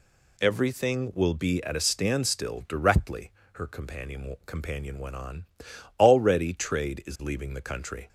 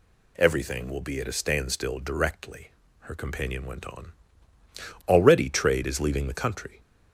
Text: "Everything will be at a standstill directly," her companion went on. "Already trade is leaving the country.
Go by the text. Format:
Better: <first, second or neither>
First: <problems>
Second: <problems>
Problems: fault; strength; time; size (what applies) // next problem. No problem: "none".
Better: second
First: says "companion" twice; at 4.4 s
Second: none